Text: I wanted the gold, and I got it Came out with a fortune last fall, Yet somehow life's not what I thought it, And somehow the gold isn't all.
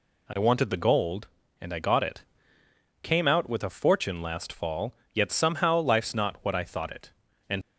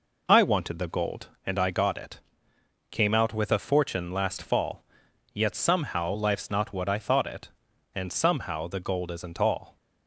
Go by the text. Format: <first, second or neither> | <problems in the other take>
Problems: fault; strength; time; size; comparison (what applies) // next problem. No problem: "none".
second | pauses between "it" and "Came"; noticeable; at 2.2 s; 0.80 s long; noticeable in the second // stops before "somehow the gold isn't all"; at 7.6 s